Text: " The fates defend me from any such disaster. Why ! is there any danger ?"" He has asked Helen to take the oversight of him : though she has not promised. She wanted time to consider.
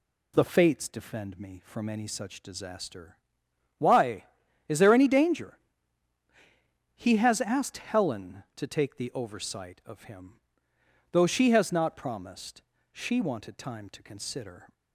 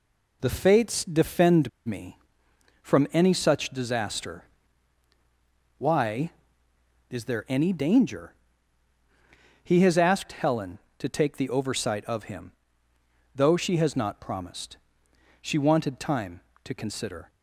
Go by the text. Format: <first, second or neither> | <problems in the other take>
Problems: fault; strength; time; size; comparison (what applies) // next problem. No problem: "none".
first | pauses between "defend" and "me"; slight; at 1.6 s; 0.17 s long